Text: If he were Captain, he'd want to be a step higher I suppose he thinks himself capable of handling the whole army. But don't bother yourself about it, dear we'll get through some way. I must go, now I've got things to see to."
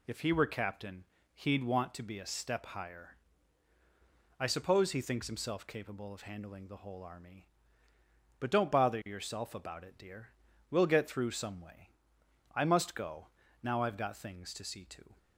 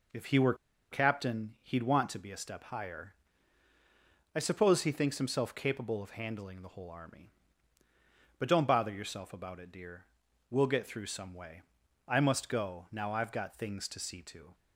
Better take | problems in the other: first | pauses between "were" and "Captain"; at 0.5 s; 0.37 s long // pauses between "higher" and "I"; at 3.1 s; 1.2 s long; also in the first // pauses between "dear" and "we'll"; at 10.0 s; 0.44 s long; also in the first

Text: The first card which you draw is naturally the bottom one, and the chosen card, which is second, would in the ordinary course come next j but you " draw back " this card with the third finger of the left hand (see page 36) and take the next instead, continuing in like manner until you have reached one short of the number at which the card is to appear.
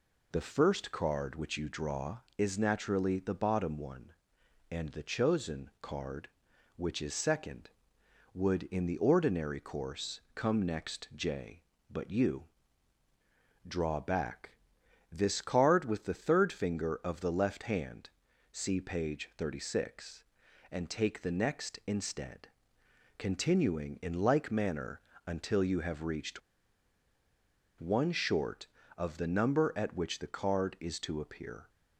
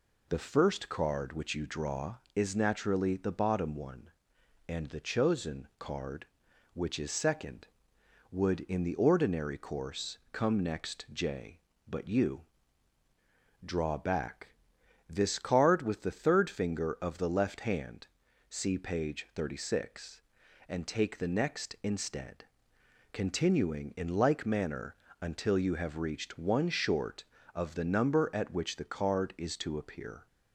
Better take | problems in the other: second | pauses between "manner" and "until"; slight; at 25.0 s; 0.24 s long; slight in the second // pauses between "reached" and "one"; strong; at 26.4 s; 1.3 s long

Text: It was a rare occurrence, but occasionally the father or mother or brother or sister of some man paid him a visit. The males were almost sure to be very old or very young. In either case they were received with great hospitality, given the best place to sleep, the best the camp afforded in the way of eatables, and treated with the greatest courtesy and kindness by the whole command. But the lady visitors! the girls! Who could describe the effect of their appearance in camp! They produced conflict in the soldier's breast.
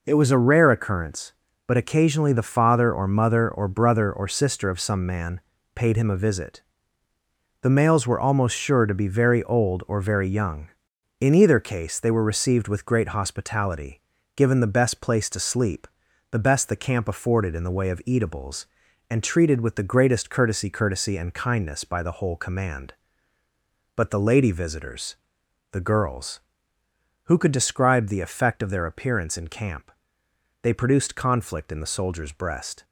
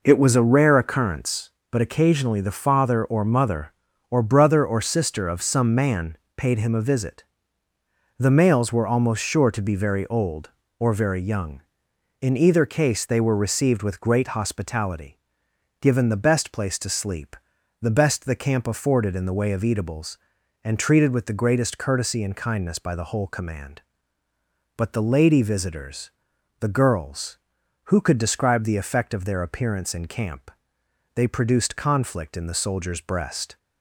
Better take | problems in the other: second | pauses between "man" and "paid"; slight; at 5.3 s; 0.34 s long; slight in the second // says "courtesy" twice; at 20.6 s

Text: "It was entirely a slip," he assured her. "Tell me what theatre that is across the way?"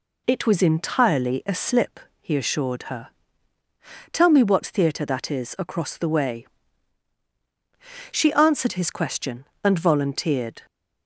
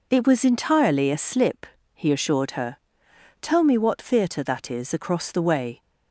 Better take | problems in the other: second | goes on to say "She answered his question and volunteered"; strong; from 8.1 s on; 2.5 s long

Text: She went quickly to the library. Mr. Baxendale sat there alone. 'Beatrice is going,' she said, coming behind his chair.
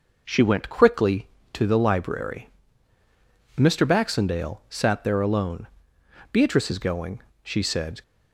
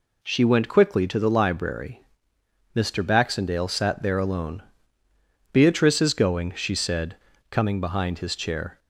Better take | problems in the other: second | stops before "coming behind his chair"; at 8.0 s

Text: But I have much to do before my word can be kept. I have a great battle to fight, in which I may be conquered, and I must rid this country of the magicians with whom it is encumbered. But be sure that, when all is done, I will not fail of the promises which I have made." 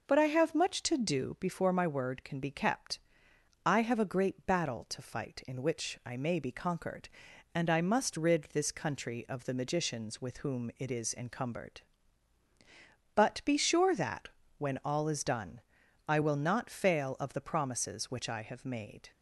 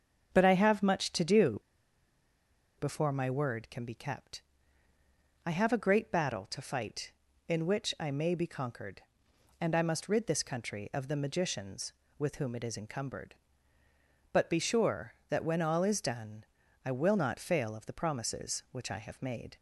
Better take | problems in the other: first | starts louder than the rest; until 1.3 s; 7 dB // pauses between "do" and "before"; at 1.5 s; 1.2 s long

